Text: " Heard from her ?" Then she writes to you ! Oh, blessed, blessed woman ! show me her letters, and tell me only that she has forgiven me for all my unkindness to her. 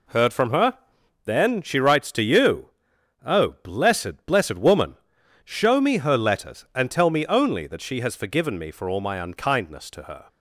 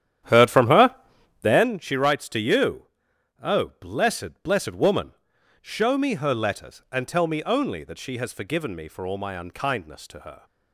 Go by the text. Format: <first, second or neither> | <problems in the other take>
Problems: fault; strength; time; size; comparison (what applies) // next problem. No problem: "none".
first | starts louder than the rest; strong; until 1.7 s; 10 dB